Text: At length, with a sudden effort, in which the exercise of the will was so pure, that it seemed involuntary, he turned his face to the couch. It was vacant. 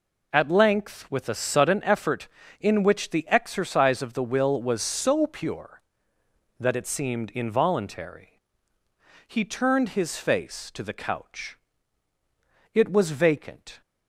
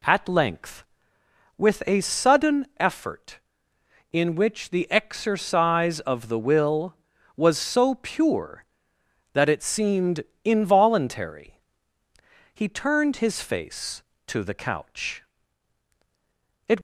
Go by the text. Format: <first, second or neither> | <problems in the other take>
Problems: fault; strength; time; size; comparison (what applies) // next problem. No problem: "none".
first | pauses between "seemed" and "involuntary"; slight; at 10.2 s; 0.22 s long // stops before "was vacant"; at 16.7 s